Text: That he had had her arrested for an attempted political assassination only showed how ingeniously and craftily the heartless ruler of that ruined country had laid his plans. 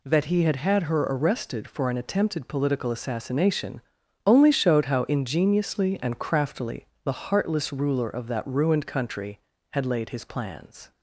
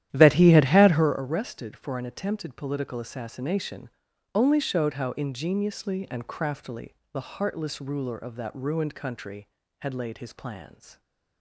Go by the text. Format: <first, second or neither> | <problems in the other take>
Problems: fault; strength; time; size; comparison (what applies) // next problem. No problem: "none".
first | starts louder than the rest; strong; until 1.2 s; 12 dB // pauses between "assassination" and "only"; at 3.8 s; 0.44 s long; also in the first // pauses between "craftily" and "the"; slight; at 6.9 s; 0.18 s long; slight in the first